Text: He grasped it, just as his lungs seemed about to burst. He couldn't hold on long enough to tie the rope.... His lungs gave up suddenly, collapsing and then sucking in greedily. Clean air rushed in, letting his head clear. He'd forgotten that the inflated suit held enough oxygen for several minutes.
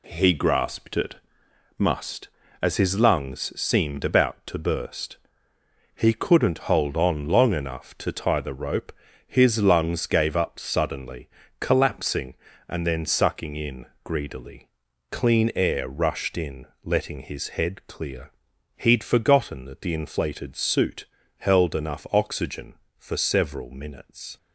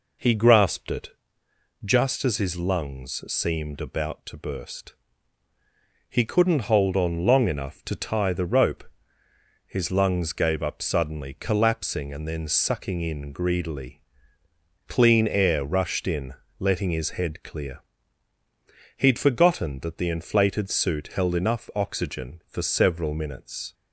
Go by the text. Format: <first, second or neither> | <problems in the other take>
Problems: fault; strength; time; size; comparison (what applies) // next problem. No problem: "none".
second | says "must" for "just"; at 1.7 s // pauses between "in" and "greedily"; slight; at 13.8 s; 0.18 s long // pauses between "suit" and "held"; slight; at 21.0 s; 0.34 s long